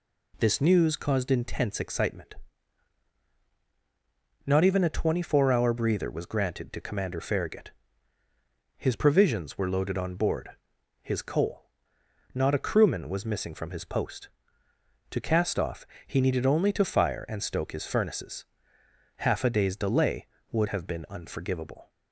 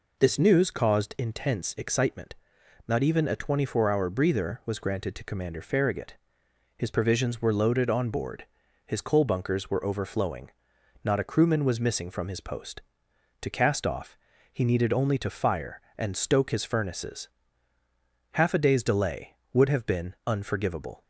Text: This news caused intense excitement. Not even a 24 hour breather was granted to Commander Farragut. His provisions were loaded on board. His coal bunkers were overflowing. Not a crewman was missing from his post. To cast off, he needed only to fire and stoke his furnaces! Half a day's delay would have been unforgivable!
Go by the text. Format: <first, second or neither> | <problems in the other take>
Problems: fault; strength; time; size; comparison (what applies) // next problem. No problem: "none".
second | skips "bunkers were overflowing"; at 11.9 s